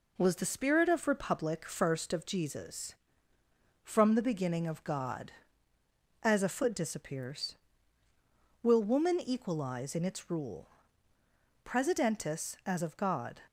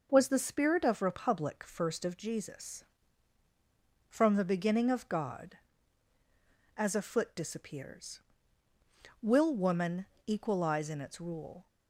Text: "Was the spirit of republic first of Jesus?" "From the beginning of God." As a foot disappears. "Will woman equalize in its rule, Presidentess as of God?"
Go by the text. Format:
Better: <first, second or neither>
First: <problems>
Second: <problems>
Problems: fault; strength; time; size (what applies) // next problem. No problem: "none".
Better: first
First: none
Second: pauses between "woman" and "equalize"; slight; at 10.0 s; 0.20 s long // stops before "Presidentess as of God"; at 11.6 s